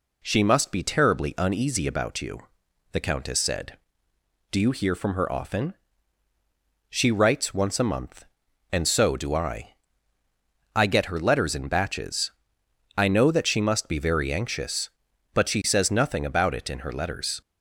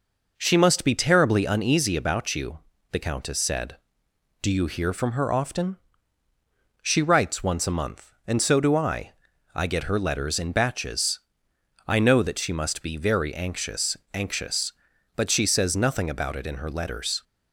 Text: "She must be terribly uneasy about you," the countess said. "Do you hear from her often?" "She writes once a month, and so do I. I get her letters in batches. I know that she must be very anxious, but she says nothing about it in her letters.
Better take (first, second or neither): first